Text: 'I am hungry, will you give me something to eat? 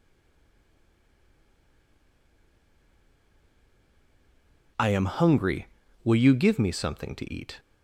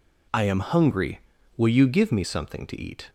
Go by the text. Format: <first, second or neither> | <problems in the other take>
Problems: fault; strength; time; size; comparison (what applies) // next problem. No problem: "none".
second | stays silent before the first word; strong; until 4.7 s; 4.7 s long